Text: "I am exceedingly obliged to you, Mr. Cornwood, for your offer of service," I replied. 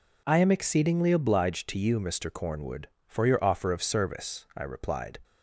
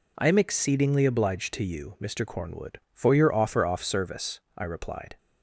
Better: first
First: none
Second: says "off" for "of"; at 3.6 s

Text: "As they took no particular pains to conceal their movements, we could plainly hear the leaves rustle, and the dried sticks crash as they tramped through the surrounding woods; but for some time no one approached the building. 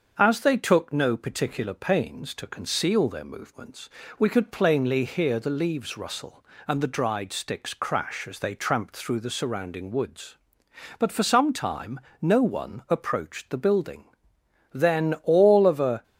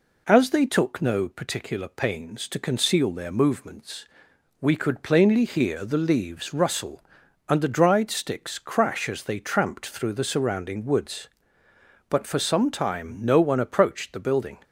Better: second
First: starts louder than the rest; until 1.1 s; 6.5 dB // pauses between "time" and "no"; slight; at 11.9 s; 0.20 s long // goes on to say "Then all of a"; noticeable; from 14.7 s on; 1.3 s long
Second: none

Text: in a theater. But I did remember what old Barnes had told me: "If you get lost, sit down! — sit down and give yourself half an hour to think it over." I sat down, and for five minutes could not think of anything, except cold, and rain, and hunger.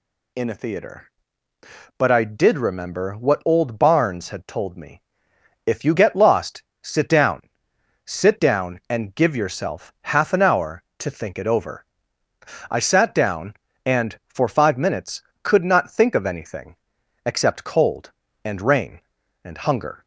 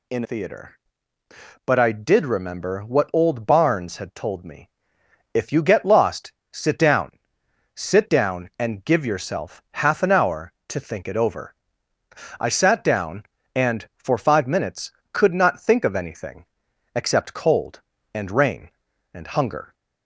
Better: first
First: none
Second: skips "a"; at 0.2 s

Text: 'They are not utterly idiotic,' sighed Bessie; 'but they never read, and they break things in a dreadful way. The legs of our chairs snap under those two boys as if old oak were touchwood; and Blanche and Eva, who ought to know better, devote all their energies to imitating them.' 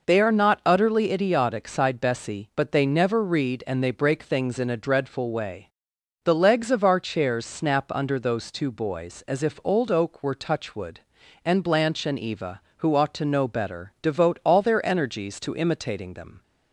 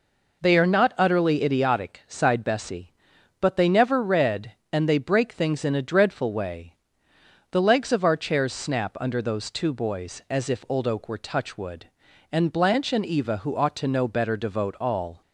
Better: first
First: none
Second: stops before "their energies to imitating them"; at 15.2 s

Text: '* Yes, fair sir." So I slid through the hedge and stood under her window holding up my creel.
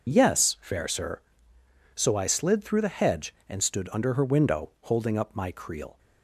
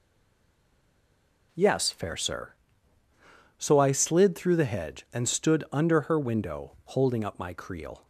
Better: first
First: none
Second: stays silent before the first word; noticeable; until 1.5 s; 1.5 s long

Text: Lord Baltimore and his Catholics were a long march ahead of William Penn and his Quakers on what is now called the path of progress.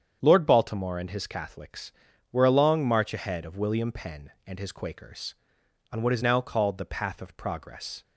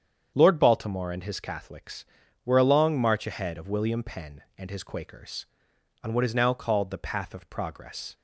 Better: neither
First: starts louder than the rest; strong; until 1.2 s; 8 dB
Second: starts louder than the rest; strong; until 1.3 s; 8 dB

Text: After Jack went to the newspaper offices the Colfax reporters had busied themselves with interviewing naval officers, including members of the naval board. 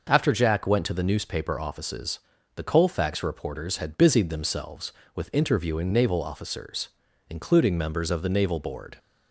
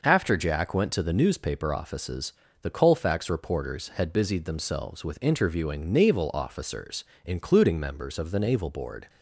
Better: neither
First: pauses between "offices" and "the"; slight; at 2.1 s; 0.36 s long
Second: pauses between "offices" and "the"; slight; at 2.3 s; 0.30 s long

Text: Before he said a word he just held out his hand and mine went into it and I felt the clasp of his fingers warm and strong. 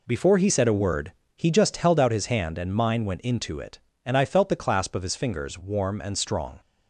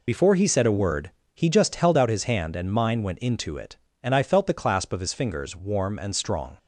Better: first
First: pauses between "word" and "he"; slight; at 1.1 s; 0.24 s long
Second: loses the start of "Before"; at 0.0 s; 35 ms // pauses between "word" and "he"; slight; at 1.1 s; 0.24 s long

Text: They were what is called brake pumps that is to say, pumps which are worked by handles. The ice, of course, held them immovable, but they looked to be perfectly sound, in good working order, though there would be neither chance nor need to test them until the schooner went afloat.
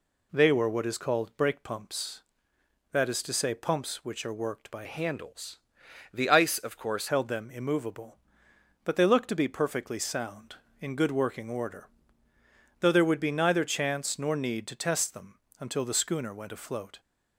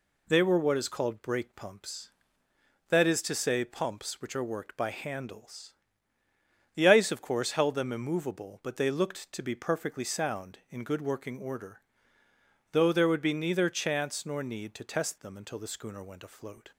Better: second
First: changes voice from "handles" to "course"; from 4.8 to 7.0 s; 2.2 s long // pauses between "them" and "until"; slight; at 15.3 s; 0.18 s long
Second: none

